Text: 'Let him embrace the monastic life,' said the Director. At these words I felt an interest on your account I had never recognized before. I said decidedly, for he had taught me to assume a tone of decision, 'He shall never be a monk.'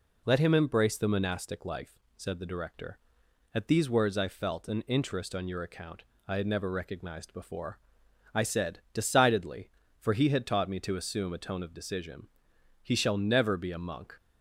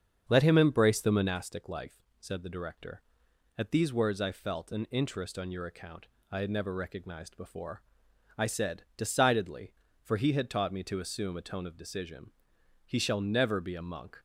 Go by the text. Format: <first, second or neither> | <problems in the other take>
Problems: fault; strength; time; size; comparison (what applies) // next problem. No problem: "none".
first | starts louder than the rest; strong; until 1.4 s; 7 dB // pauses between "account" and "I"; slight; at 6.0 s; 0.24 s long; slight in the first